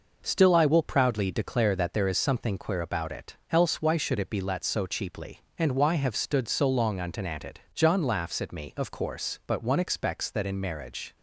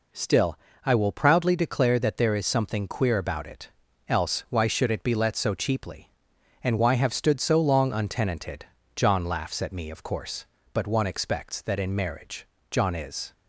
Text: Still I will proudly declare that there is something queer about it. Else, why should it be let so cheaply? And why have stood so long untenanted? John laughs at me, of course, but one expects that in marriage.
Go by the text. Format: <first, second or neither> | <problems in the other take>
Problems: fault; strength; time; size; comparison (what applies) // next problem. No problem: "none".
first | pauses between "Still" and "I"; slight; at 0.5 s; 0.26 s long // goes on to say "John is"; noticeable; from 12.7 s on; 0.62 s long